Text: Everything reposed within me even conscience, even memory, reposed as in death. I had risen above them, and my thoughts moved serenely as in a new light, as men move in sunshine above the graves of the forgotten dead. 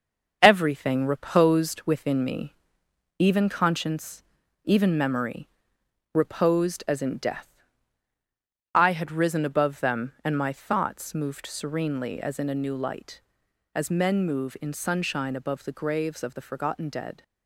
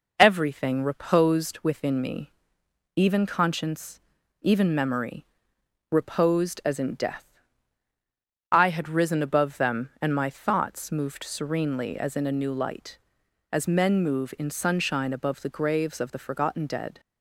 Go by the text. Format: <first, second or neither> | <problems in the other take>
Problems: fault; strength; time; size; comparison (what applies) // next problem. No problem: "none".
second | gets quieter; noticeable; throughout; 6 dB // pauses between "me" and "even"; noticeable; at 2.5 s; 0.66 s long; noticeable in the second